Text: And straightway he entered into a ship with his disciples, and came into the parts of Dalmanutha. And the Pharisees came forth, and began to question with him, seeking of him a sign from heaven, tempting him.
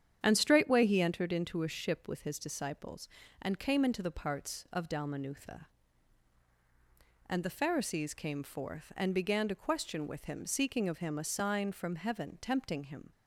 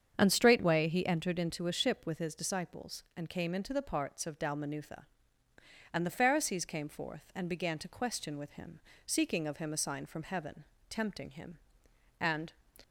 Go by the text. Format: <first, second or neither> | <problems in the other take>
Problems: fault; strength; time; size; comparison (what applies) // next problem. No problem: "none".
first | starts louder than the rest; strong; until 1.1 s; 7.5 dB; strong in the first // goes on to say "And"; slight; from 12.1 s on; 0.34 s long